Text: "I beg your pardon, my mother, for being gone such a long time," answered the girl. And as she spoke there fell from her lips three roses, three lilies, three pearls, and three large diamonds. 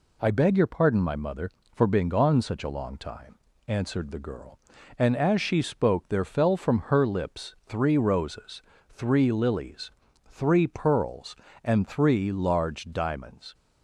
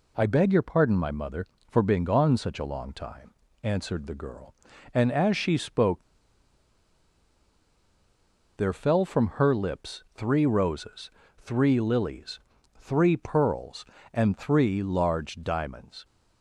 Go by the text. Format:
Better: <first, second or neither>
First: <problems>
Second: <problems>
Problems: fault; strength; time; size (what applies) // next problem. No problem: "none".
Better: first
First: none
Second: pauses between "spoke" and "there"; strong; at 6.0 s; 2.5 s long